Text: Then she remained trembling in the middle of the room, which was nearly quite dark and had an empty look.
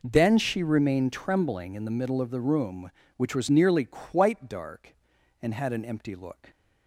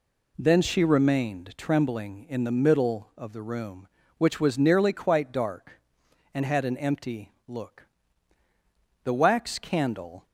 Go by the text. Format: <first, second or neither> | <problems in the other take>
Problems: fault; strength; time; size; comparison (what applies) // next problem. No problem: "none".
first | pauses between "empty" and "look"; slight; at 7.3 s; 0.16 s long // goes on to say "The wax candle"; noticeable; from 9.0 s on; 1.2 s long